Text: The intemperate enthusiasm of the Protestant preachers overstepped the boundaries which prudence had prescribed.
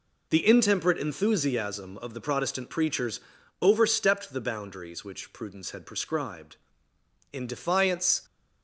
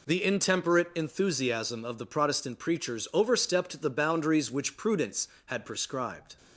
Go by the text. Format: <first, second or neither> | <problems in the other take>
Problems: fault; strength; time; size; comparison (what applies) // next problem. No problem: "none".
second | pauses between "preachers" and "overstepped"; at 3.1 s; 0.42 s long // goes on to say "In defiance"; noticeable; from 7.3 s on; 0.90 s long